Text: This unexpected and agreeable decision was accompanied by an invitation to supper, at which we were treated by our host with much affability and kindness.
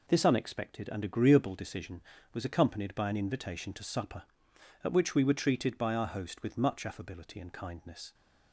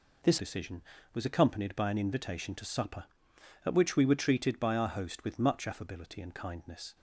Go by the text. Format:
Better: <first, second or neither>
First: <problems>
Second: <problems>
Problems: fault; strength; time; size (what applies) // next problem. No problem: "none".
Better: first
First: none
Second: skips "unexpected and agreeable"; at 0.3 s